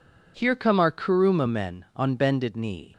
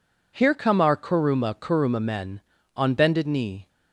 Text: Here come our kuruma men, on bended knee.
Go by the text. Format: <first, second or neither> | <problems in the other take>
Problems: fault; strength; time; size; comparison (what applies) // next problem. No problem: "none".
first | says "kuruma" twice; at 1.5 s